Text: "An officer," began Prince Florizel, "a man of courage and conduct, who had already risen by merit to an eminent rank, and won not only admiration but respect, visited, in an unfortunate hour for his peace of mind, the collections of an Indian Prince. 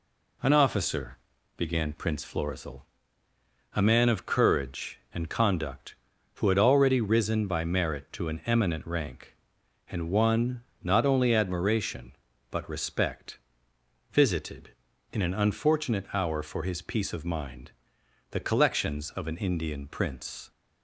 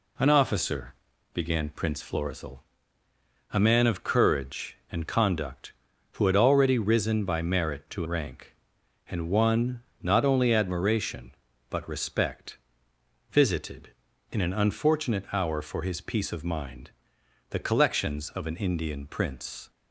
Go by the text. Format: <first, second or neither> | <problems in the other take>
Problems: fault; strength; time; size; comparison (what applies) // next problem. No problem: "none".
first | skips "an eminent"; at 8.0 s // pauses between "won" and "not"; slight; at 9.8 s; 0.18 s long; slight in the first